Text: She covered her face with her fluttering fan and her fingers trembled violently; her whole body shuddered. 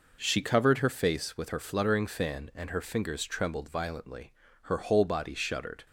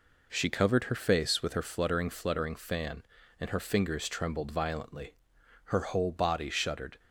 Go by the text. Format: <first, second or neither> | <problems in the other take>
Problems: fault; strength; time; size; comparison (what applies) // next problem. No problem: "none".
first | says "fluttering" twice; at 2.0 s